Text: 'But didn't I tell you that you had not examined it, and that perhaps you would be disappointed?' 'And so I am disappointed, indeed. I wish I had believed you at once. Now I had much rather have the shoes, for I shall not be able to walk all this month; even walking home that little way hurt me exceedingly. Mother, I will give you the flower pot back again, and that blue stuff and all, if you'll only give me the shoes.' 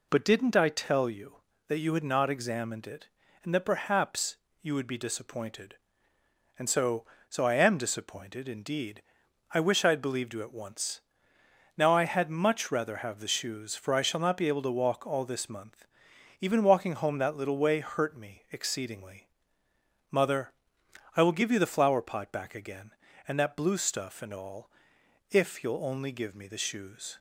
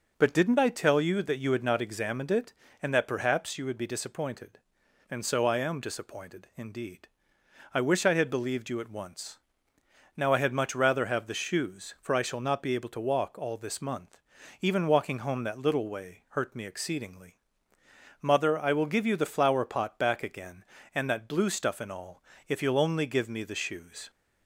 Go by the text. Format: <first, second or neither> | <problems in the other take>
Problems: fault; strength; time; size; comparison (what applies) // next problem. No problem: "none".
second | pauses between "perhaps" and "you"; slight; at 4.3 s; 0.26 s long // says "so" twice; at 7.3 s